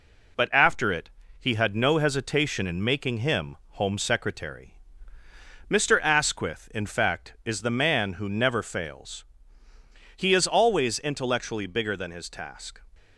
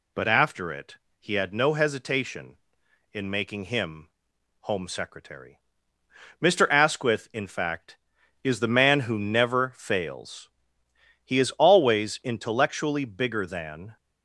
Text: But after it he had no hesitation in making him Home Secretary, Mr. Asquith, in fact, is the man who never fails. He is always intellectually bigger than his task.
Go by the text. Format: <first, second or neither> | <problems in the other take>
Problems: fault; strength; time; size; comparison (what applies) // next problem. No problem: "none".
first | pauses between "it" and "he"; slight; at 0.9 s; 0.24 s long; slight in the first // pauses between "him" and "Home"; noticeable; at 4.0 s; 0.52 s long; slight in the first // stops before "his task"; at 13.9 s